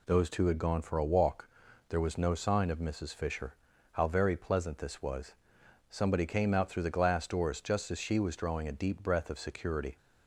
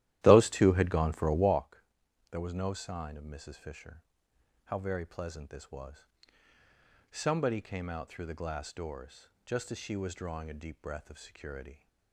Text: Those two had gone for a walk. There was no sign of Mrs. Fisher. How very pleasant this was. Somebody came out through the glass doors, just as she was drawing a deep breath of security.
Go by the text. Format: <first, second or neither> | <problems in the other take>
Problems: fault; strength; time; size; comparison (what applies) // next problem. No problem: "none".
first | starts louder than the rest; strong; until 1.7 s; 13.5 dB